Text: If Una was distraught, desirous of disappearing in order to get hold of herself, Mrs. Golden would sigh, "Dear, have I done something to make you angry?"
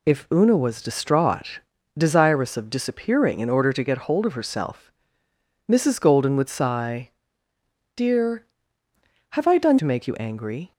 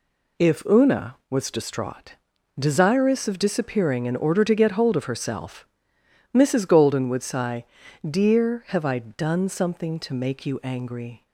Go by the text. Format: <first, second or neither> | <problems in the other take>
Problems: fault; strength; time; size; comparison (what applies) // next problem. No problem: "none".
second | skips "something"; at 9.7 s